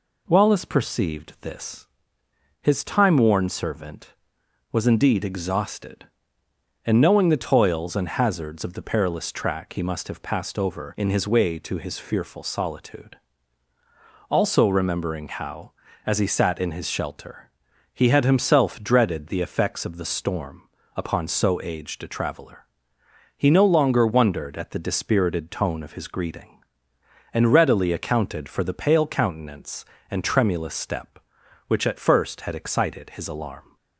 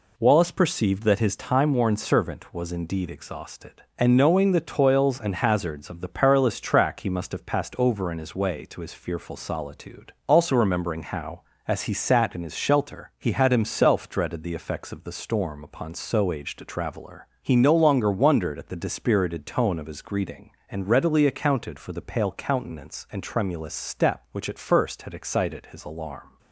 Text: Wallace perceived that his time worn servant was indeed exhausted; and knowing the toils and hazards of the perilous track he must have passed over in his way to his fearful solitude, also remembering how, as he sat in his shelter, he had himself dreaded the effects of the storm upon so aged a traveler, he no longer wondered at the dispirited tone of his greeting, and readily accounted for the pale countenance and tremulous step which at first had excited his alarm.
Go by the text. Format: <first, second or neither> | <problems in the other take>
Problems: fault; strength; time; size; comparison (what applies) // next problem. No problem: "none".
second | says "this" for "that"; at 1.4 s // pauses between "storm" and "upon"; slight; at 20.6 s; 0.28 s long